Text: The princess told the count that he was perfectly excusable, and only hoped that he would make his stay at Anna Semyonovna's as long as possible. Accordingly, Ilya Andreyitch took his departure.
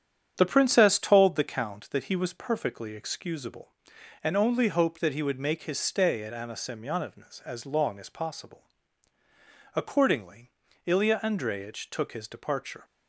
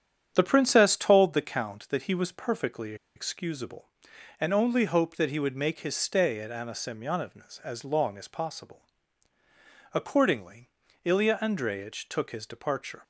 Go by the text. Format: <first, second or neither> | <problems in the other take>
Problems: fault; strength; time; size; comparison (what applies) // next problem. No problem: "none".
first | starts louder than the rest; strong; until 1.3 s; 8.5 dB; strong in the first // pauses between "perfectly" and "excusable"; slight; at 2.9 s; 0.21 s long